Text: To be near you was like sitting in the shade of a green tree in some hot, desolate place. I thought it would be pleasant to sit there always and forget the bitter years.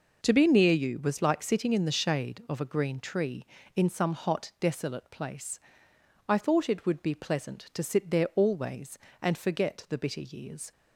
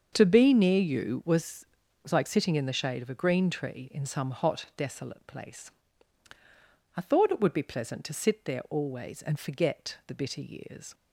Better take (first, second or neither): first